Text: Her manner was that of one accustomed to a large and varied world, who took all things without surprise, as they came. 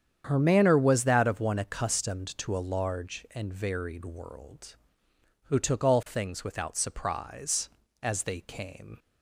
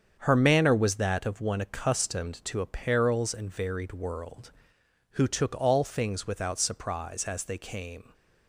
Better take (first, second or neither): first